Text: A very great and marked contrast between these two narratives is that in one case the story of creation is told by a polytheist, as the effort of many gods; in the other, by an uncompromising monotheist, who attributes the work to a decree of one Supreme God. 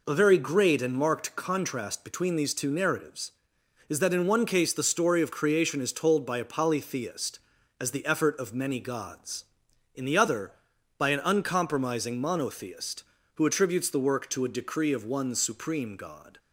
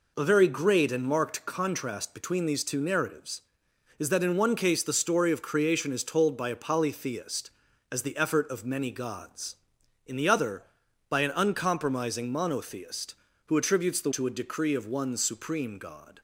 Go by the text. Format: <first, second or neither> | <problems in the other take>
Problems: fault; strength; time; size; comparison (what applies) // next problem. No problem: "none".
first | skips "work"; at 14.1 s